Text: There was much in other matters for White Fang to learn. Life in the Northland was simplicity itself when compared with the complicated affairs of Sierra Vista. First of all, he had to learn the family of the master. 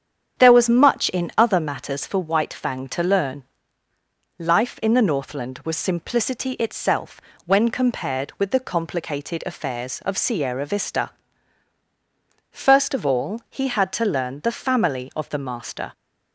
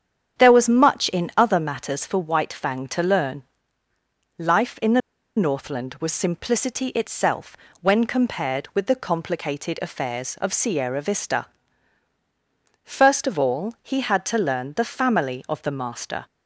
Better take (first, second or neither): first